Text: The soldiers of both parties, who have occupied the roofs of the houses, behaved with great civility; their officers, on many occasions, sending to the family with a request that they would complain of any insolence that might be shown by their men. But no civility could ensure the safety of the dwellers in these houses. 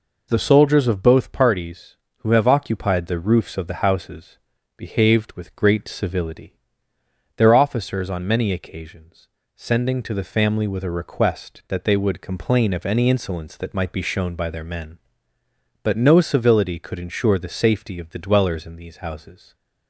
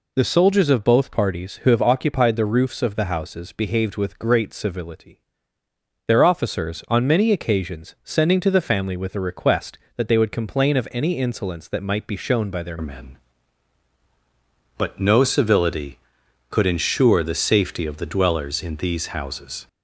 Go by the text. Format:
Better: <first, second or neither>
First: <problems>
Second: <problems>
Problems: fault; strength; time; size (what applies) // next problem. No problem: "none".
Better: first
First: none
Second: changes voice at "men"; from 12.8 s on; 6.8 s long